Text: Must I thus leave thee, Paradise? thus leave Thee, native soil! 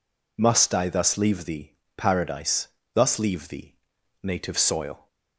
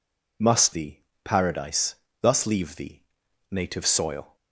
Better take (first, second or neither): first